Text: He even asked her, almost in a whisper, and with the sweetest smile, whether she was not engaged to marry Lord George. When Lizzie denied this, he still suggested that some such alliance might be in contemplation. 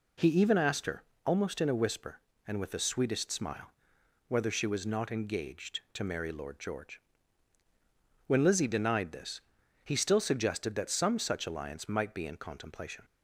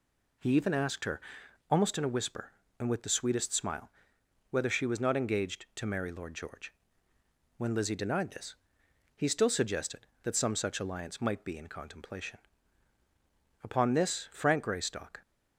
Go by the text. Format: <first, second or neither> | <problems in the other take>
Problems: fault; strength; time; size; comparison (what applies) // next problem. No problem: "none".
first | goes on to say "Upon this Frank Greystock"; from 13.6 s on; 1.5 s long